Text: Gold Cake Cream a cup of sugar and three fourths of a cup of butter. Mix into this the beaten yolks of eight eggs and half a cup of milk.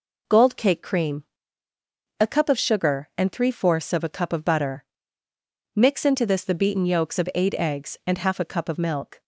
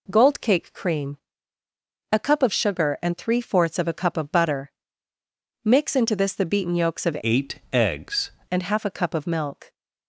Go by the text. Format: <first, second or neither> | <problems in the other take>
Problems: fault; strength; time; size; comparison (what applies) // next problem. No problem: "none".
first | pauses between "Cream" and "a"; noticeable; at 1.1 s; 0.96 s long; noticeable in the first // changes voice from "eight" to "eggs"; from 7.2 to 8.3 s; 1.1 s long